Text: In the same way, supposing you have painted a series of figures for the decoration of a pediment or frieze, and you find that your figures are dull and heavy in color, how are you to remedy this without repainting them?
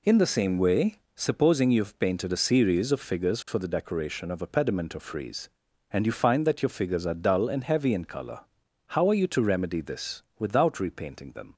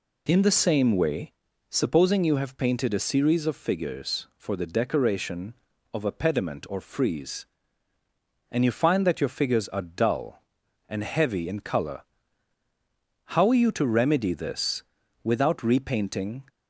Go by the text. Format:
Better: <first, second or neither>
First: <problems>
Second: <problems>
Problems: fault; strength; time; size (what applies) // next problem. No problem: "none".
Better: first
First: pauses between "this" and "without"; slight; at 10.2 s; 0.16 s long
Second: pauses between "this" and "without"; at 14.8 s; 0.42 s long // stops before "them"; at 16.4 s